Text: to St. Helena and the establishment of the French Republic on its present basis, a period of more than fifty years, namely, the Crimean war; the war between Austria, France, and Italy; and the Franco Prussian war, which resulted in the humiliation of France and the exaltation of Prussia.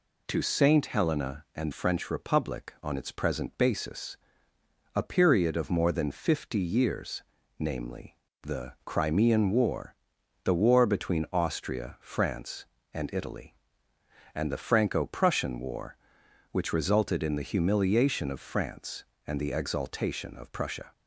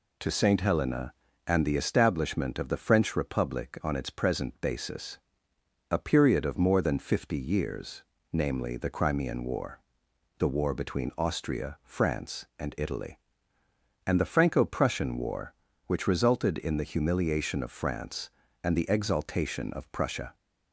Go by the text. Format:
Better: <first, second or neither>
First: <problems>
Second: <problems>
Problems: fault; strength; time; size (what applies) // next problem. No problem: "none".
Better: second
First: skips "the establishment of the"; at 1.7 s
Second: none